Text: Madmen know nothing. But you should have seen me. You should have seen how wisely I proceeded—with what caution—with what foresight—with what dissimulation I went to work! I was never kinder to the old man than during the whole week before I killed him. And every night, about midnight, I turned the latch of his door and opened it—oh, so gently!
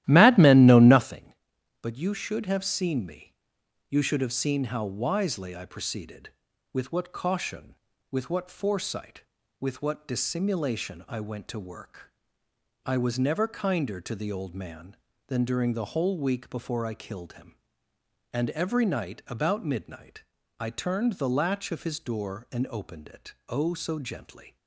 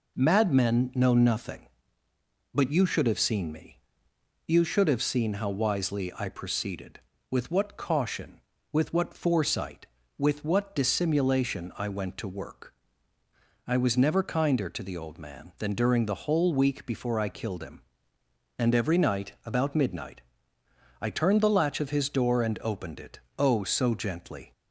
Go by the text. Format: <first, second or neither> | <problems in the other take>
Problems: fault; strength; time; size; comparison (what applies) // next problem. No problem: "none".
second | starts louder than the rest; strong; until 1.2 s; 14 dB